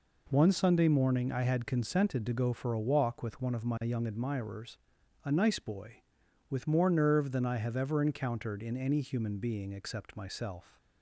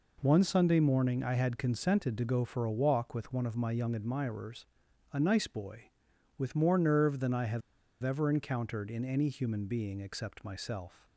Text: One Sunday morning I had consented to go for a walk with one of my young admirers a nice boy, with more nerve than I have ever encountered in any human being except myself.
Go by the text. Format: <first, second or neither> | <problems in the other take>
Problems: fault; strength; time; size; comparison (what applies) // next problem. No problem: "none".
first | pauses between "admirers" and "a"; noticeable; at 4.6 s; 0.48 s long; noticeable in the first // pauses between "have" and "ever"; at 7.6 s; 0.42 s long